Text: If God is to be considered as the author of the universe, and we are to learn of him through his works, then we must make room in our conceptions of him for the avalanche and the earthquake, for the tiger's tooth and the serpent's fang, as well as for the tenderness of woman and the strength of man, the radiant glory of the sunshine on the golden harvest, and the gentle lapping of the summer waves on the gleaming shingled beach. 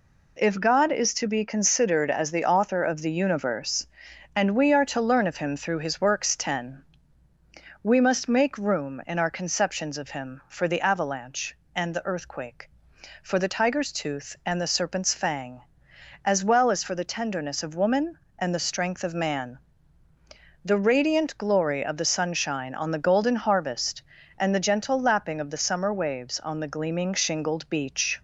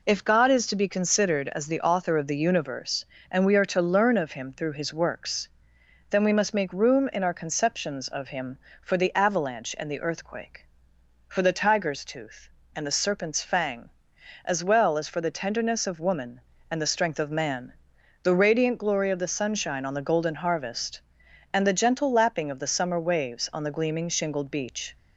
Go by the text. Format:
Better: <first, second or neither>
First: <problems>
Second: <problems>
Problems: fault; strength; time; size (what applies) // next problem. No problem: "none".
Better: second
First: says "ten" for "then"; at 6.3 s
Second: none